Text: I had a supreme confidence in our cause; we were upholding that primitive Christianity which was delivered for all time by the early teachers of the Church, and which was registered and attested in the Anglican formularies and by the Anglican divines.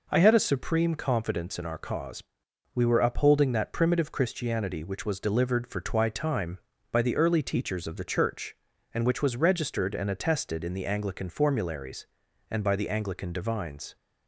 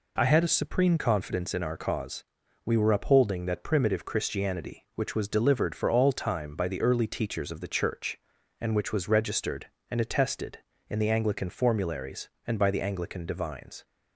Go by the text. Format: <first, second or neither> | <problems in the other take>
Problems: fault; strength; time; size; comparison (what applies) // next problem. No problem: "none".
second | says "twi" for "all"; at 5.8 s